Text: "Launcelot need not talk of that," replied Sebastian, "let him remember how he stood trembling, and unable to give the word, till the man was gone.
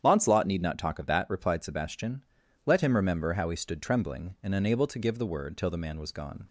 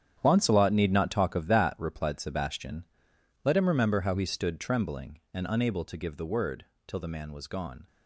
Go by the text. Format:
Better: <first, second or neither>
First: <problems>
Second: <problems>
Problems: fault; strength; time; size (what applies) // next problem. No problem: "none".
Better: first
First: starts louder than the rest; strong; until 1.0 s; 9 dB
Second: gets quieter; strong; throughout; 13 dB // starts louder than the rest; strong; until 1.2 s; 9.5 dB